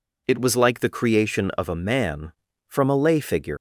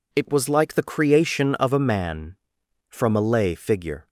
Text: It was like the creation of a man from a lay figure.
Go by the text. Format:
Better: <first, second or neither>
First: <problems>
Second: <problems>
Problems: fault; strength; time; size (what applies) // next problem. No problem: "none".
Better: second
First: leaves "figure" unfinished; at 3.5 s; 110 ms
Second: none